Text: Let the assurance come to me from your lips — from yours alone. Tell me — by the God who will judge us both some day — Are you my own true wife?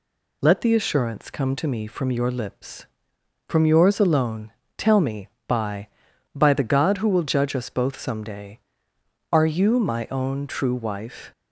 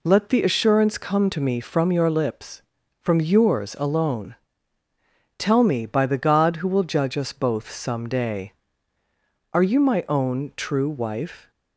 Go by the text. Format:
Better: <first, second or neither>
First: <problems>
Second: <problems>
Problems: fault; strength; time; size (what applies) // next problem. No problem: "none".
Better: second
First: says "by" twice; at 6.3 s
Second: none